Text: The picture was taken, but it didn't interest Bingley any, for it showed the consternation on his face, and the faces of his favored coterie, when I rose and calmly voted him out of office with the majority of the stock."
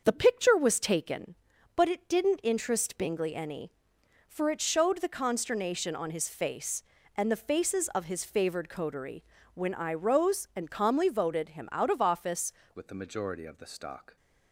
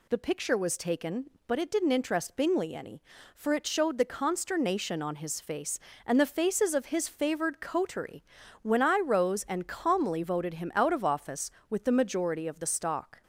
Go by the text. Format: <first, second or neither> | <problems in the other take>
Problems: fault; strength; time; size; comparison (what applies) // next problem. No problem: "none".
second | starts louder than the rest; until 1.0 s; 6.5 dB // changes voice at "with"; from 12.7 s on; 1.4 s long